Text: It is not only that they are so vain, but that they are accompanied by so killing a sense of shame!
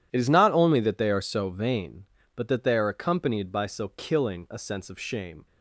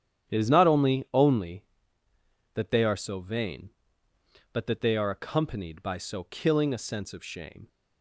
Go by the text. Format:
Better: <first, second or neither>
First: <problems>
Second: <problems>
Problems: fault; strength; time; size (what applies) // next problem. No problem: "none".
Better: first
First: none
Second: starts louder than the rest; strong; until 1.3 s; 10 dB // says "only" twice; at 1.1 s